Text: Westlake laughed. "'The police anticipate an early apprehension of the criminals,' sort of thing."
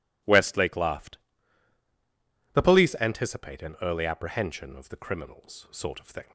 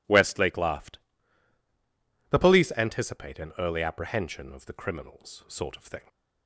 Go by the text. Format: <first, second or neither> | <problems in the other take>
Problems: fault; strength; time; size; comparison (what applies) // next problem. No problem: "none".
neither | none